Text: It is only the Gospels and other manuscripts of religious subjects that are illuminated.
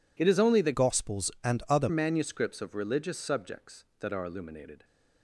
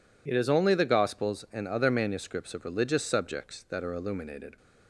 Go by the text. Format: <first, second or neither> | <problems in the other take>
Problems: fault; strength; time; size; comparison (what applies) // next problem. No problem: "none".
second | changes voice from "Gospels" to "other"; from 0.7 to 1.8 s; 1.1 s long